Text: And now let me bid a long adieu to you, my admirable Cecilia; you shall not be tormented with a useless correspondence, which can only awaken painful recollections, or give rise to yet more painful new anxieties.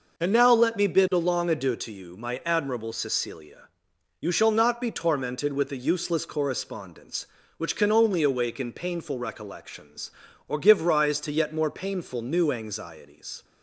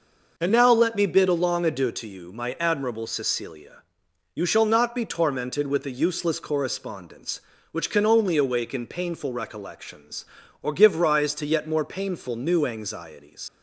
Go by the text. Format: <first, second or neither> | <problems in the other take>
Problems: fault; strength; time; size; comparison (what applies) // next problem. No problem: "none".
first | leaves "anxieties" unfinished; at 13.4 s; 95 ms